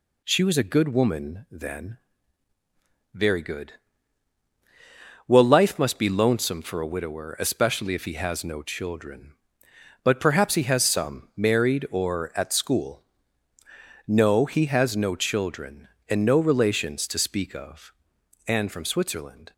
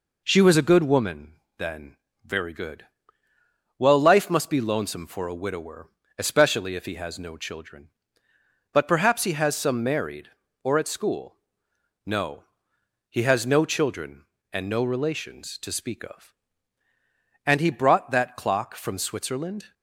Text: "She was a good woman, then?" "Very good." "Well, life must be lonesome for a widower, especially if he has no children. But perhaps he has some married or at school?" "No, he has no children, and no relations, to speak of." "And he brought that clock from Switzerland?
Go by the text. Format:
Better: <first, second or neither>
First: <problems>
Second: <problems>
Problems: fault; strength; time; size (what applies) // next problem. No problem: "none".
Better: second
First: skips "he brought that clock"; at 18.7 s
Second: none